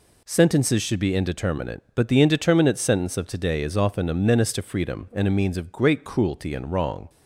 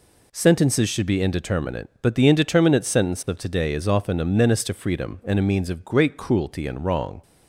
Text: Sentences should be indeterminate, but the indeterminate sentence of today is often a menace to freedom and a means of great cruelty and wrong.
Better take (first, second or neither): neither